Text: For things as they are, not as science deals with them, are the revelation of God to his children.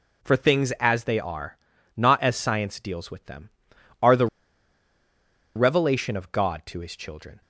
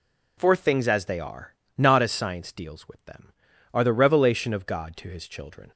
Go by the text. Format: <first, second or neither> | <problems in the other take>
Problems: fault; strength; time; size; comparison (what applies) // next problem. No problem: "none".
second | pauses between "the" and "revelation"; strong; at 4.2 s; 1.2 s long